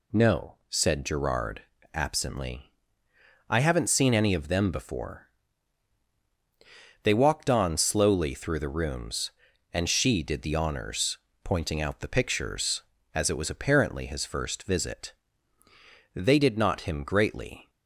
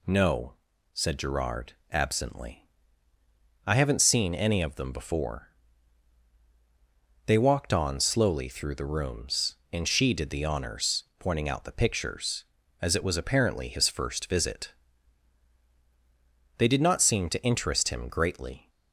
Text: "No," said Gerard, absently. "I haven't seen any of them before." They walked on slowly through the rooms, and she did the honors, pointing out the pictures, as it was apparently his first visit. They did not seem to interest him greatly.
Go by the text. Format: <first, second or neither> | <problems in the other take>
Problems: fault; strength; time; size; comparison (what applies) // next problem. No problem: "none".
second | skips "seem to interest"; at 16.8 s